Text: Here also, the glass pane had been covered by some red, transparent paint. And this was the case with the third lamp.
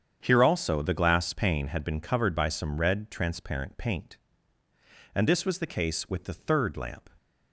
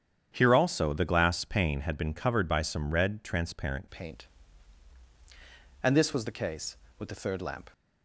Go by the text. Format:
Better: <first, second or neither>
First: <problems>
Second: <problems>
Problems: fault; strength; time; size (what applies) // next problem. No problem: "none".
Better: first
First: starts louder than the rest; strong; until 1.2 s; 8 dB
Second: starts louder than the rest; strong; until 1.3 s; 8.5 dB // changes voice at "paint"; from 3.9 s on; 3.8 s long